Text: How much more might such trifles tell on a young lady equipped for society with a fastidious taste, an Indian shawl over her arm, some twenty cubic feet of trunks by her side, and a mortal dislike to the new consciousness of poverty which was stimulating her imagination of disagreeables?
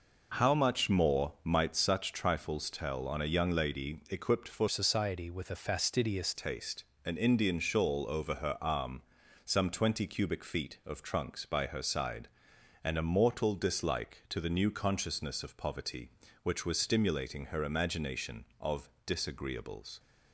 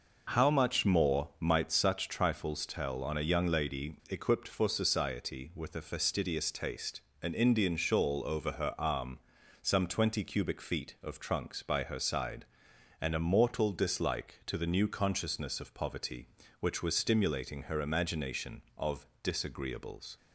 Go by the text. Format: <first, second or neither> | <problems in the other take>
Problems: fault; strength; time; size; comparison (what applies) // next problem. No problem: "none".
second | changes voice from "society" to "fastidious"; from 4.6 to 6.3 s; 1.7 s long // pauses between "of" and "disagreeables"; slight; at 18.8 s; 0.16 s long; slight in the second